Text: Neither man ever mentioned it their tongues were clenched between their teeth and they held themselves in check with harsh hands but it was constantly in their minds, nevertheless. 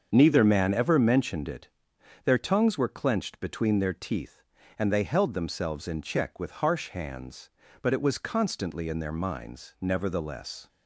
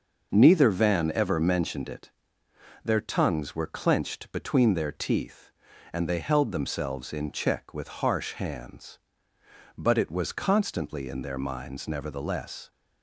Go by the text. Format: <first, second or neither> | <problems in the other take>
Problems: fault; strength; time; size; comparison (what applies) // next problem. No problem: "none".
first | starts louder than the rest; noticeable; until 1.3 s; 6 dB; also in the first // says "van" for "man"; at 0.6 s // pauses between "it" and "their"; noticeable; at 2.0 s; 0.74 s long; noticeable in the first